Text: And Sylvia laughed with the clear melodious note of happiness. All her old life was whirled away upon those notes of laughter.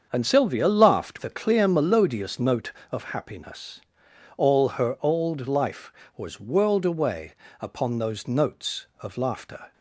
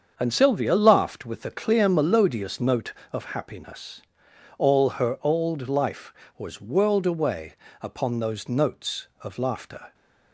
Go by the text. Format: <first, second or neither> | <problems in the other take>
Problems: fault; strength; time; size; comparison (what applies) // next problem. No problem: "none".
second | starts louder than the rest; until 1.1 s; 7 dB; also in the second // skips "with"; at 1.1 s // pauses between "away" and "upon"; slight; at 7.3 s; 0.28 s long; slight in the second